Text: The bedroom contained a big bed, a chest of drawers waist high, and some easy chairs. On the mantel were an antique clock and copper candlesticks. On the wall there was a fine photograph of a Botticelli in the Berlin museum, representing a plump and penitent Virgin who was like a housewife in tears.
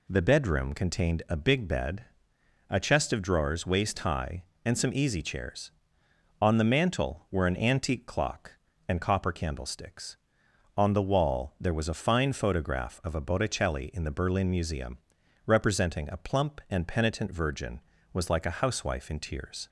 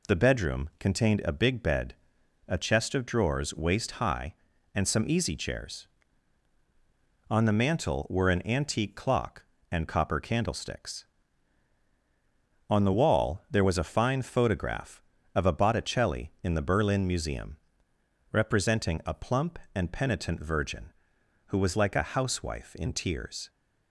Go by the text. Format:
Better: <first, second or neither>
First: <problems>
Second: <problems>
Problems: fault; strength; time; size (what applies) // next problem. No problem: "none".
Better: second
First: skips "who"; at 17.9 s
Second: none